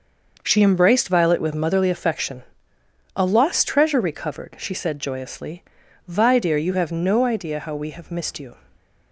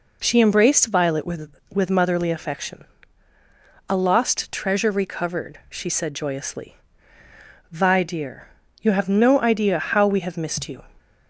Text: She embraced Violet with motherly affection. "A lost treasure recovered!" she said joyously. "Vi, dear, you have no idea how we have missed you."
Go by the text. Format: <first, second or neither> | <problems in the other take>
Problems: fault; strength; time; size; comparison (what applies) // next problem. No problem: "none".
first | says "with" twice; at 1.7 s